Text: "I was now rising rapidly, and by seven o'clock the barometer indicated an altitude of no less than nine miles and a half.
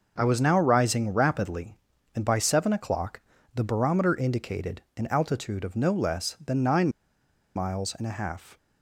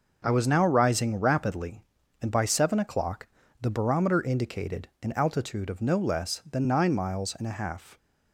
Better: second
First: pauses between "o'clock" and "the"; slight; at 3.2 s; 0.32 s long // pauses between "indicated" and "an"; slight; at 4.8 s; 0.16 s long // pauses between "nine" and "miles"; noticeable; at 6.8 s; 0.66 s long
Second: pauses between "o'clock" and "the"; slight; at 3.2 s; 0.32 s long

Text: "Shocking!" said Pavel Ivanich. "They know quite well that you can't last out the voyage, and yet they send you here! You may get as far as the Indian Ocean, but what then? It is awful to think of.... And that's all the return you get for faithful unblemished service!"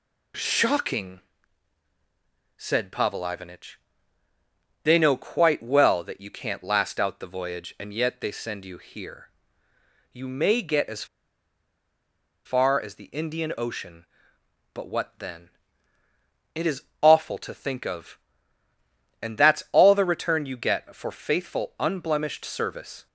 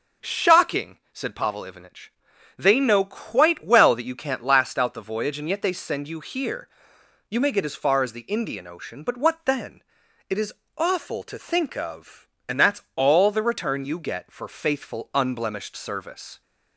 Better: second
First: pauses between "as" and "far"; strong; at 11.0 s; 1.3 s long // pauses between "is" and "awful"; slight; at 16.8 s; 0.18 s long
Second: pauses between "is" and "awful"; slight; at 10.5 s; 0.24 s long

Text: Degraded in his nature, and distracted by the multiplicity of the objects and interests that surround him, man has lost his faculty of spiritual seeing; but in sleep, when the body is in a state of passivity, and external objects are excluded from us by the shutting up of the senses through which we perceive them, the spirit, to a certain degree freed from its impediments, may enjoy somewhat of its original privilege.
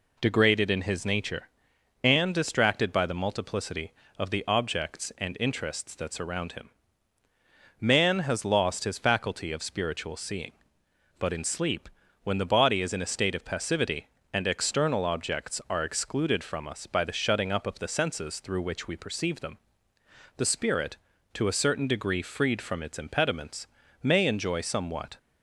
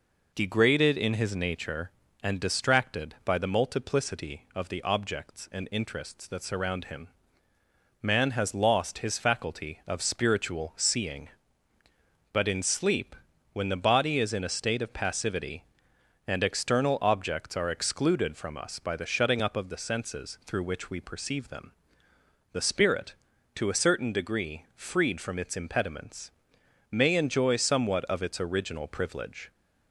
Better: second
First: stops before "of its original privilege"; at 25.1 s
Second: none

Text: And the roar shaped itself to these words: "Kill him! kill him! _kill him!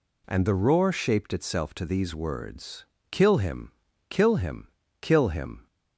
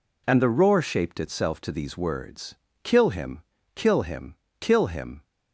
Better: neither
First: none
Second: none

